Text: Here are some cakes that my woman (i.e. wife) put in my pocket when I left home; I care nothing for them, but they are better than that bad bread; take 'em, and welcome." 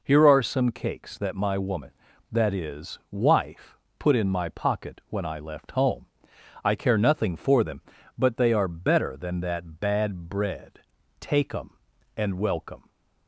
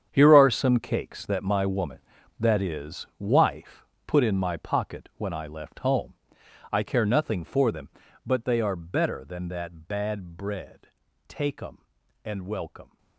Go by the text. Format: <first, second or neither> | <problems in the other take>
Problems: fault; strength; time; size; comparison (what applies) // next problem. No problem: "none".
first | gets quieter; strong; throughout; 15 dB